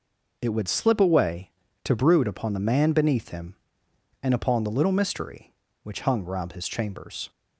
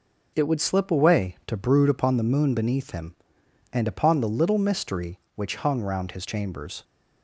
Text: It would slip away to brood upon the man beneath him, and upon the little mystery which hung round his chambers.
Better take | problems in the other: first | says "moon" for "man"; at 2.2 s

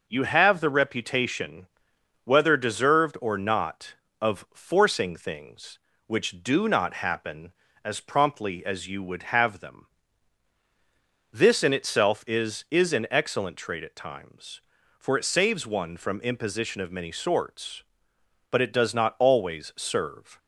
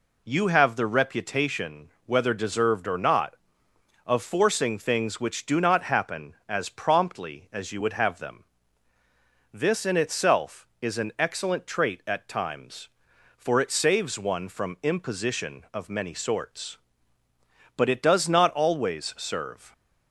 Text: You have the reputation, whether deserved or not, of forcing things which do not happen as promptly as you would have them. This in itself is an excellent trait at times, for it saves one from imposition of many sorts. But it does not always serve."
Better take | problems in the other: second | says "is" twice; at 12.6 s

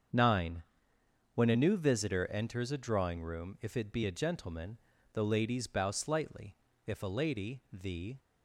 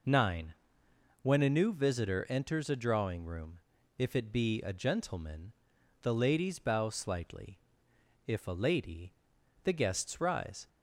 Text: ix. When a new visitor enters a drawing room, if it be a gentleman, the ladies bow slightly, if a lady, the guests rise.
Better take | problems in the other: second | starts louder than the rest; until 1.8 s; 7 dB // stops before "guests rise"; at 8.1 s

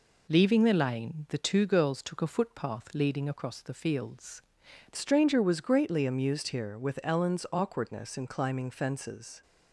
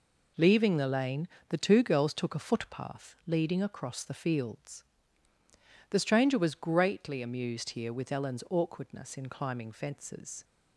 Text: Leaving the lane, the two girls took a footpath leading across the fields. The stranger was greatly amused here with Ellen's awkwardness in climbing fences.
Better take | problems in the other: second | changes voice at "stranger"; from 4.9 s on; 4.5 s long

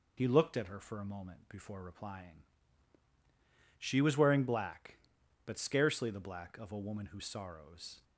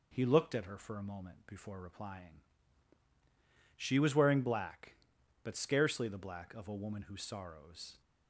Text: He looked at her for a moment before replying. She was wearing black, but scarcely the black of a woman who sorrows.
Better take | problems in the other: second | loses the start of "He"; at 0.1 s; 40 ms

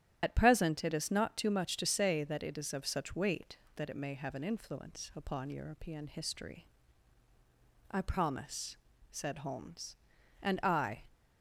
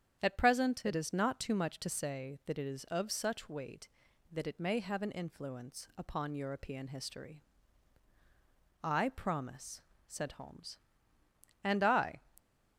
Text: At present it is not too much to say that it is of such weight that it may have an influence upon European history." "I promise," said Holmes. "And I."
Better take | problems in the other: second | loses the start of "At"; at 0.2 s; 40 ms // starts louder than the rest; strong; until 1.2 s; 10.5 dB; strong in the second

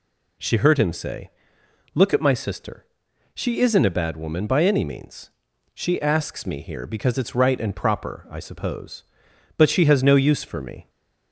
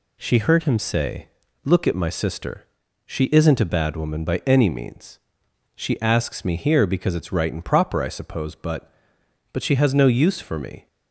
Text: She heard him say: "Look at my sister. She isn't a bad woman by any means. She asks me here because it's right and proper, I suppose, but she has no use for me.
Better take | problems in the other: first | says "but" twice; at 9.5 s

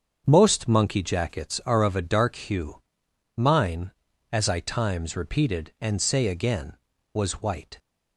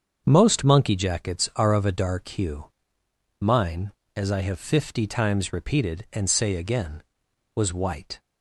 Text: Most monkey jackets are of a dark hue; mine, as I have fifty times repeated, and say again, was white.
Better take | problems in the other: second | starts louder than the rest; until 1.2 s; 7 dB; also in the second // skips "have fifty"; at 4.6 s

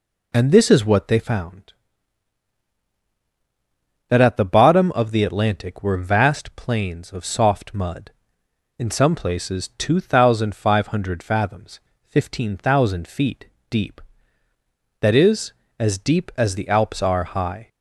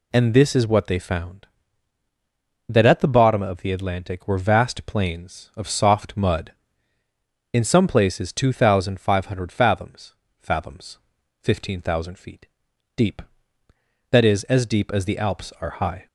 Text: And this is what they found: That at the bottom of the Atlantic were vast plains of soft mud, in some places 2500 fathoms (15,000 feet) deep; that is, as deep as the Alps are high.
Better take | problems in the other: first | says "fathoms" twice; at 10.4 s

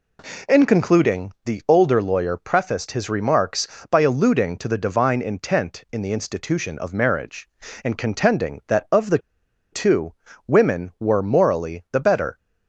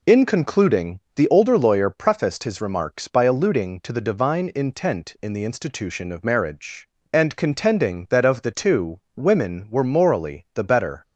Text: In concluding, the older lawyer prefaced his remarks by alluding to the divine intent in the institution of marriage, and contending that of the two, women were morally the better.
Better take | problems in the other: second | pauses between "the" and "two"; noticeable; at 9.1 s; 0.53 s long

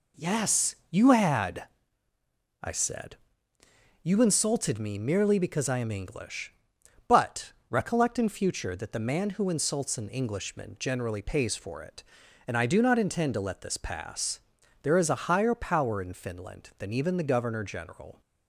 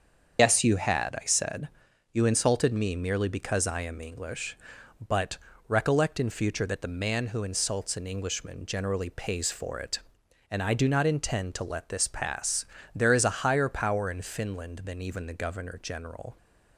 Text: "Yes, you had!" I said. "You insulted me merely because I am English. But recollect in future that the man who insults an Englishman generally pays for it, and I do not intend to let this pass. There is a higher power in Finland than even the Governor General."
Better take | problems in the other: first | loses the start of "Yes"; at 0.3 s; 150 ms // starts louder than the rest; until 1.4 s; 7 dB // pauses between "But" and "recollect"; slight; at 5.3 s; 0.30 s long; slight in the first

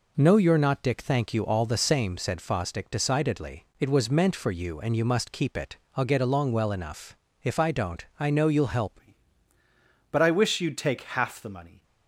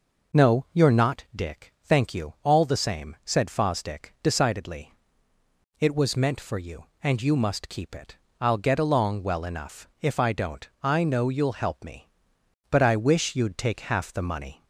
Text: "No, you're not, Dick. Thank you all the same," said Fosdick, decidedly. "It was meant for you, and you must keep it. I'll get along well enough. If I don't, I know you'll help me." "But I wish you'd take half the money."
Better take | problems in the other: second | changes voice at "me"; from 9.0 s on; 2.8 s long

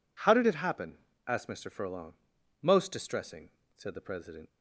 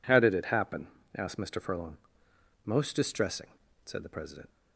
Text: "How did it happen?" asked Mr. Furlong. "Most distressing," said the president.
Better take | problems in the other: neither | none

